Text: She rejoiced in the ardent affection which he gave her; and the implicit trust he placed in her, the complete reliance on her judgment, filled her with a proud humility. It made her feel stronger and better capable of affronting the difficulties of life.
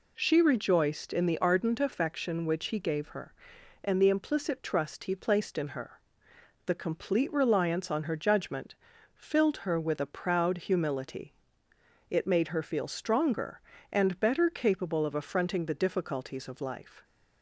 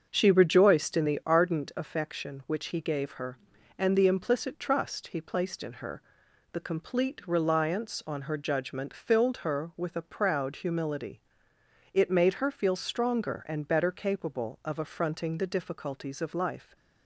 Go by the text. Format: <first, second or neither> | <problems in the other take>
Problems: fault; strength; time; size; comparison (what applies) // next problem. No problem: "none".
first | starts louder than the rest; until 1.3 s; 6.5 dB